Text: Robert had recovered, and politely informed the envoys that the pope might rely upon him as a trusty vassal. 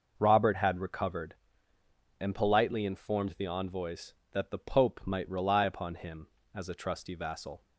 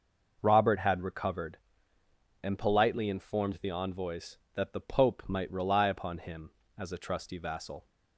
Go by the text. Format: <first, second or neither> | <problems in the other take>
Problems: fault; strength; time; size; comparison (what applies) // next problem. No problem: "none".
neither | none